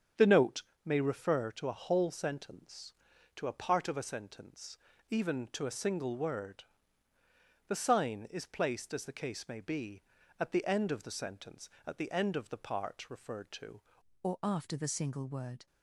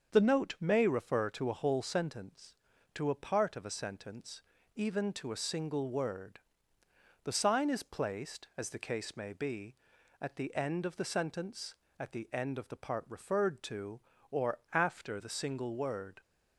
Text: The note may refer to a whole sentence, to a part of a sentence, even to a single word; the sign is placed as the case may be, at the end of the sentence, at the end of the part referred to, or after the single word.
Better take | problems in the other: second | starts louder than the rest; strong; until 1.4 s; 7.5 dB; also in the second // pauses between "note" and "may"; slight; at 0.6 s; 0.24 s long // changes voice at "or"; from 14.2 s on; 1.4 s long

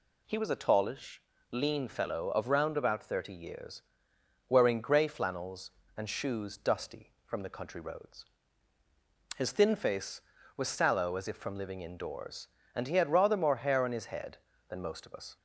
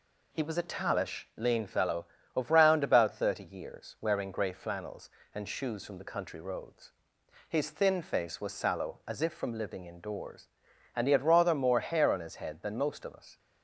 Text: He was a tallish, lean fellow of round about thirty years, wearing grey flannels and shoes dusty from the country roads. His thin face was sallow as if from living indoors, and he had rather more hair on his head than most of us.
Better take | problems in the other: first | skips "dusty"; at 5.8 s

